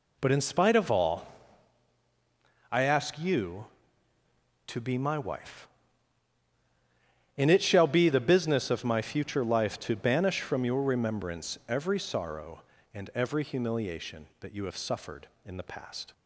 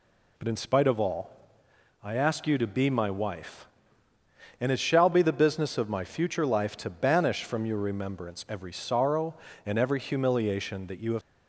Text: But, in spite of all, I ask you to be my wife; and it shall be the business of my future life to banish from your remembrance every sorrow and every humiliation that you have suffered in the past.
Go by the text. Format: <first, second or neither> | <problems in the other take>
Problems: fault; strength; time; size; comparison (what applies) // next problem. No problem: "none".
first | stops before "suffered in the past"; at 11.2 s